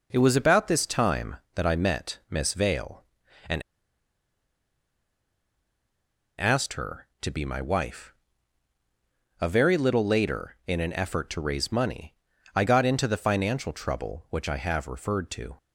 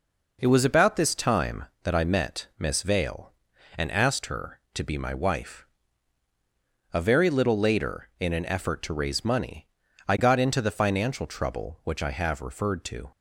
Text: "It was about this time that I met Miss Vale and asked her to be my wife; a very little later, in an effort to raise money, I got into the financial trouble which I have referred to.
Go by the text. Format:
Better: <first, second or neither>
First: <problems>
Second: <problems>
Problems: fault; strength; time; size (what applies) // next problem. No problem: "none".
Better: second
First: pauses between "and" and "asked"; strong; at 3.6 s; 2.7 s long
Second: none